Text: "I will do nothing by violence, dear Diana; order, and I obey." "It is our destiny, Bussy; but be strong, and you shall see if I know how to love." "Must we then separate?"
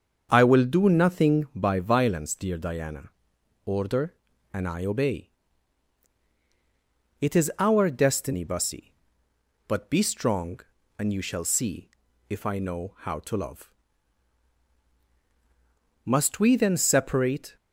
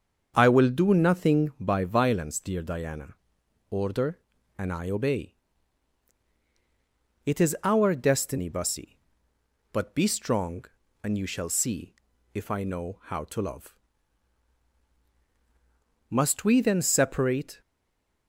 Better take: first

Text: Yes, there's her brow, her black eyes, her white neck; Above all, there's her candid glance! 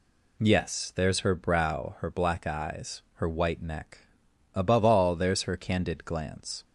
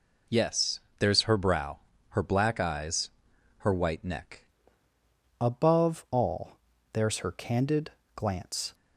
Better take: first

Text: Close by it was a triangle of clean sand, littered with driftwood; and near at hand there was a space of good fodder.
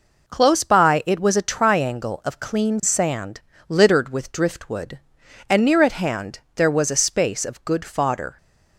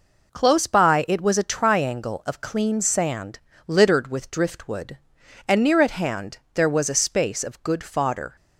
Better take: neither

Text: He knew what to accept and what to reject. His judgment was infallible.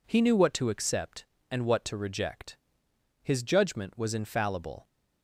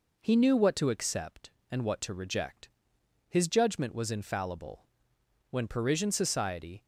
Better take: first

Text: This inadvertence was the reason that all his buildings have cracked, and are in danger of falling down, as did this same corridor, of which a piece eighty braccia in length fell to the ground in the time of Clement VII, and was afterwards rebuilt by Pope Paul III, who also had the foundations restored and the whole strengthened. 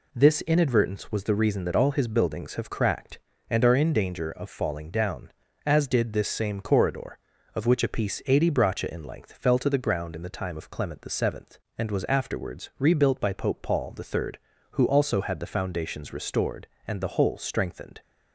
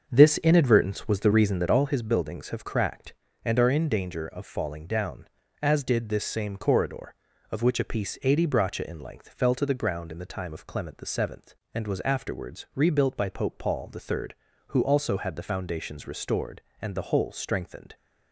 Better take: first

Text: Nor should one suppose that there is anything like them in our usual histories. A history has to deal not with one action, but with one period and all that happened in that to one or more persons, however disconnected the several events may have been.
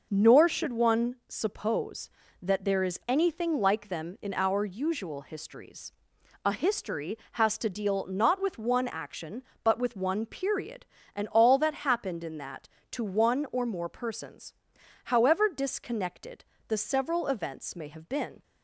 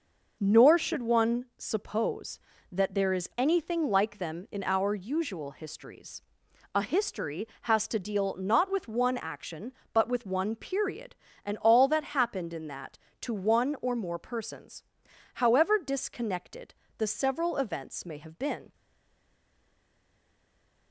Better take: first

